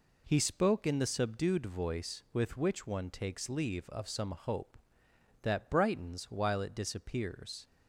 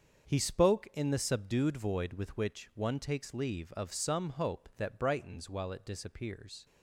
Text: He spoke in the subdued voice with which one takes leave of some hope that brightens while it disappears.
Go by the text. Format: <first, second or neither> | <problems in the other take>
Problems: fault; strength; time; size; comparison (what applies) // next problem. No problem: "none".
first | starts louder than the rest; until 1.3 s; 7 dB // says "void" for "voice"; at 1.7 s